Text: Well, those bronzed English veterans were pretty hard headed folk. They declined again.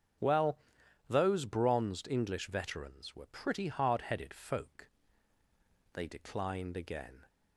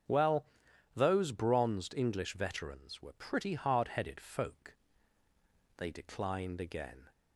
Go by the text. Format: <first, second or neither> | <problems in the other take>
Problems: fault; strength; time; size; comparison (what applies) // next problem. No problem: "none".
neither | starts louder than the rest; strong; the same in both